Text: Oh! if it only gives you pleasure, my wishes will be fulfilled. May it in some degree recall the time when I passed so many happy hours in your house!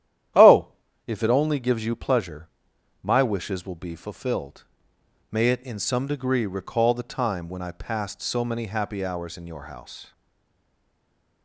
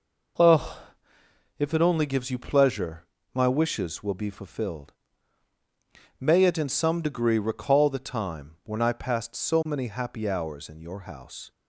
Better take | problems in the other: second | starts louder than the rest; strong; until 1.7 s; 11 dB // stays silent after the last word; noticeable; from 10.1 s on; 1.3 s long

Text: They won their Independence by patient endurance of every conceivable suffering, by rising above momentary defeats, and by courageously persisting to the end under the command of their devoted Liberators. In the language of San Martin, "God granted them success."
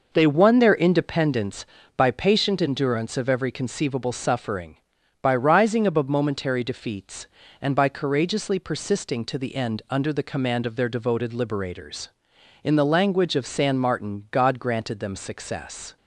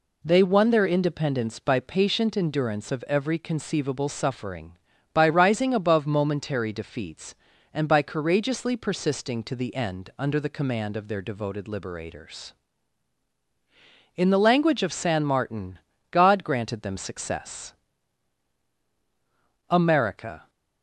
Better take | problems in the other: first | goes on to say "AMERICA"; noticeable; from 19.6 s on; 0.80 s long

